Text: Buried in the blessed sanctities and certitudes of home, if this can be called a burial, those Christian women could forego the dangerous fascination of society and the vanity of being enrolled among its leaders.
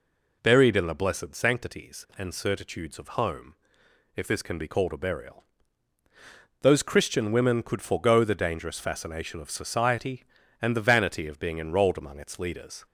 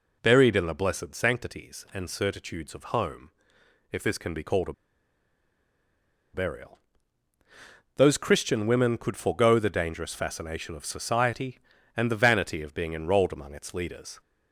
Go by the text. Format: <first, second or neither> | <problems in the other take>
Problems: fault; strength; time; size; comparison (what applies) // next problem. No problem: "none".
first | pauses between "a" and "burial"; strong; at 4.7 s; 1.6 s long